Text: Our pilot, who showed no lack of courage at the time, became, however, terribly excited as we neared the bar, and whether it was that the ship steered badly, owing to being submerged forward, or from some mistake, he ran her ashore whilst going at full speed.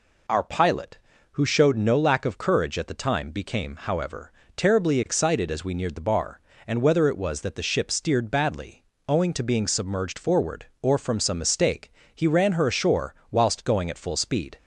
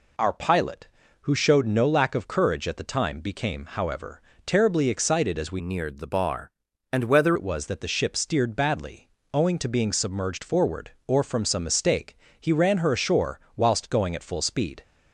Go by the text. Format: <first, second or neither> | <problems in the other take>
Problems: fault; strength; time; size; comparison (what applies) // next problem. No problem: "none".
first | changes voice from "neared" to "whether"; from 5.6 to 7.3 s; 1.7 s long // pauses between "ashore" and "whilst"; slight; at 13.3 s; 0.16 s long; slight in the first